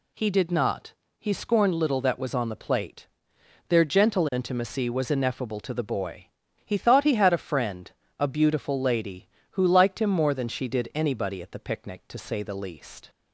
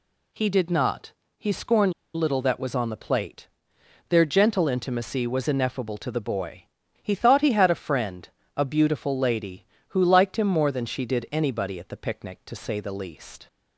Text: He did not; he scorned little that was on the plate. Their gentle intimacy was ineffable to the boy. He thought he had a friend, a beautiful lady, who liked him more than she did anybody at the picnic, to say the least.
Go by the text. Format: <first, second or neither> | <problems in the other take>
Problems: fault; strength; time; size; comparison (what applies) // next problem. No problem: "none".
first | pauses between "scorned" and "little"; slight; at 1.9 s; 0.22 s long